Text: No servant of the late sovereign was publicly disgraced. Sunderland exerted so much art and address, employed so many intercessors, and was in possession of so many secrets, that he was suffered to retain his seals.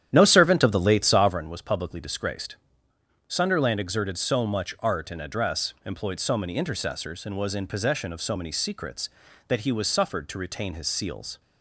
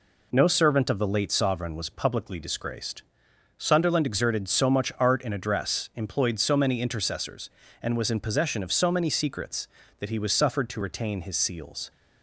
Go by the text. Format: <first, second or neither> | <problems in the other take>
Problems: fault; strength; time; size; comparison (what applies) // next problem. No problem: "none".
second | starts louder than the rest; strong; until 1.4 s; 10.5 dB